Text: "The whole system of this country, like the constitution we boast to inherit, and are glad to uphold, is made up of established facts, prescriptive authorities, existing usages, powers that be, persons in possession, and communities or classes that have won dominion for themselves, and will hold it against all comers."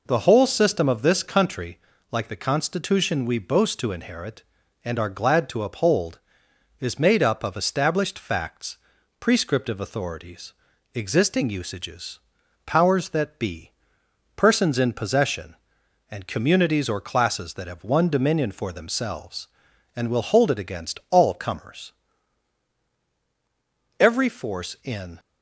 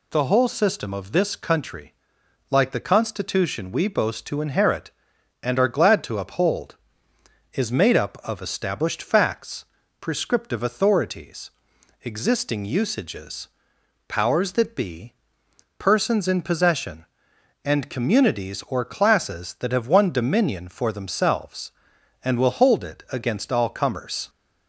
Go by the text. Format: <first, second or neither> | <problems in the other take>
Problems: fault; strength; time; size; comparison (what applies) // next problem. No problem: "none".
second | goes on to say "Every force in"; noticeable; from 23.9 s on; 1.2 s long